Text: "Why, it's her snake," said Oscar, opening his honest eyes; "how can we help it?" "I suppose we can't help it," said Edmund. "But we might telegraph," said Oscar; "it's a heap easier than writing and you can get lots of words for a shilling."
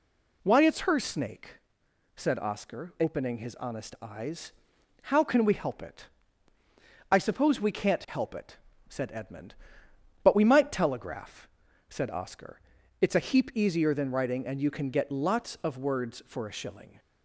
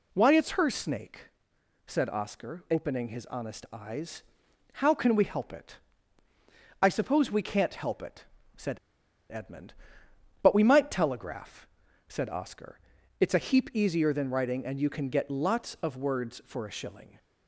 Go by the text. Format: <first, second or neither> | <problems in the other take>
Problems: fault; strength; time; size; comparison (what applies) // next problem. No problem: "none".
first | pauses between "said" and "Edmund"; noticeable; at 8.7 s; 0.53 s long